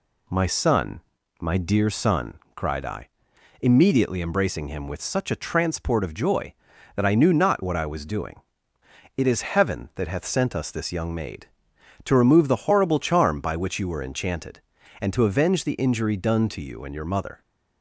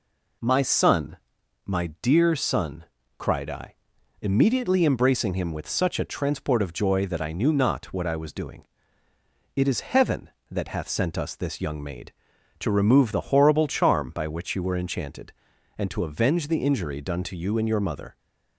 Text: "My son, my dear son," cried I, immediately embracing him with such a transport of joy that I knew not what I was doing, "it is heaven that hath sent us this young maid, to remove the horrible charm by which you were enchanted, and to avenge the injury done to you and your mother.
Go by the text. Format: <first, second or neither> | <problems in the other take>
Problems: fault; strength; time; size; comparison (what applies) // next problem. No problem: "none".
neither | none